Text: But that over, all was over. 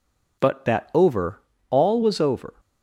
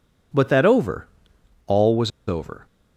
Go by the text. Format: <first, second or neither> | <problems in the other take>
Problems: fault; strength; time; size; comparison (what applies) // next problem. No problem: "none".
first | pauses between "was" and "over"; slight; at 2.1 s; 0.17 s long